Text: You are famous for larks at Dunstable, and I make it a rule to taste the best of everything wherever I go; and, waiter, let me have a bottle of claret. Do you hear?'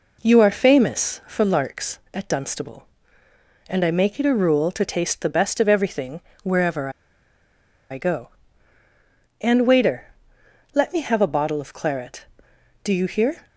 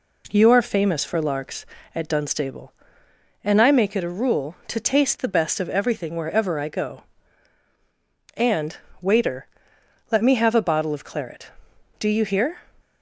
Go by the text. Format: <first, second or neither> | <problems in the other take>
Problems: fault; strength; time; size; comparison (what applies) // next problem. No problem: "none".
second | pauses between "everything" and "wherever"; slight; at 6.1 s; 0.24 s long // pauses between "wherever" and "I"; at 6.8 s; 1.0 s long